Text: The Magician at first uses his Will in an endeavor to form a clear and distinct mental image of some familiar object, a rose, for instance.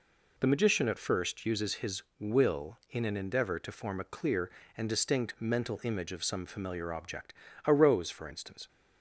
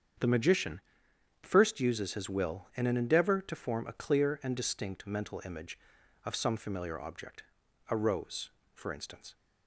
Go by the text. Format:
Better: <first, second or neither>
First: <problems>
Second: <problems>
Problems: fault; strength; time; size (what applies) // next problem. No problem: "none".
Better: first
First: none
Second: starts louder than the rest; strong; until 1.8 s; 7.5 dB // skips "at"; at 1.1 s